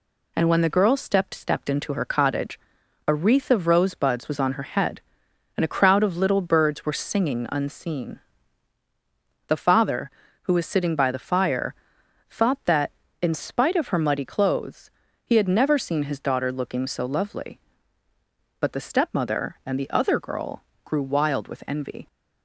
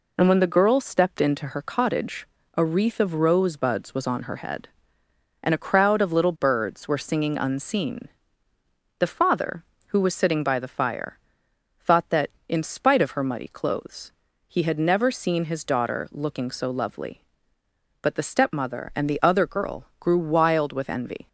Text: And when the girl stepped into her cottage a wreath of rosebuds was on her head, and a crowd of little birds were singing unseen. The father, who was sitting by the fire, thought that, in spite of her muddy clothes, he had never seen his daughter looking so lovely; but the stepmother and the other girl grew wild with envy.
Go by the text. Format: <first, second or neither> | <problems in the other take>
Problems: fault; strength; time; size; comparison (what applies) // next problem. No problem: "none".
second | says "stepped" twice; at 1.3 s // pauses between "cottage" and "a"; noticeable; at 2.5 s; 0.49 s long; slight in the second // pauses between "girl" and "grew"; slight; at 20.6 s; 0.22 s long